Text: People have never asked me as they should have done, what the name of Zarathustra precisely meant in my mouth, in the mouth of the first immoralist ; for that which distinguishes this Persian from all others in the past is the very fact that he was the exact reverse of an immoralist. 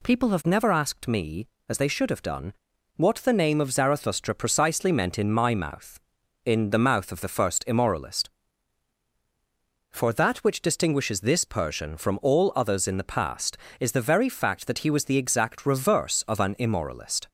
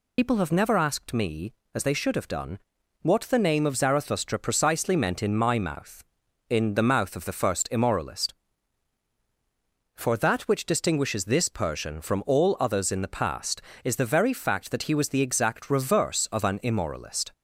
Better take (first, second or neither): first